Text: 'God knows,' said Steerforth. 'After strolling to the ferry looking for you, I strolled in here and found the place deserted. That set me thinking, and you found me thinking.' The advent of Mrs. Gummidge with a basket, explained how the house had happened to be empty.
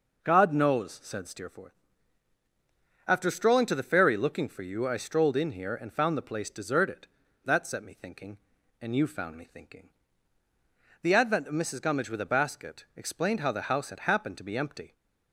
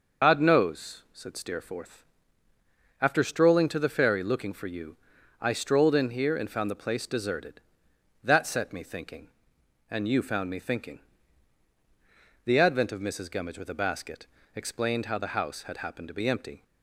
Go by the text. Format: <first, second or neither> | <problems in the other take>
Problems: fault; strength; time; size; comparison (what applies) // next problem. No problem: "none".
first | loses the start of "God"; at 0.2 s; 95 ms // starts louder than the rest; noticeable; until 1.3 s; 6 dB